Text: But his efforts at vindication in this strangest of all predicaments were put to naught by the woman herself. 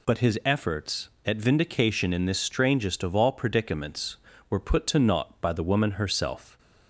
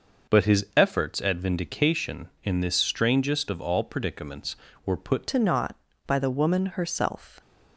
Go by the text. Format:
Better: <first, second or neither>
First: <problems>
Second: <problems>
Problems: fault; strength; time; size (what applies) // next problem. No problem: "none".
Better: first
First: none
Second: changes voice at "to"; from 5.2 s on; 2.2 s long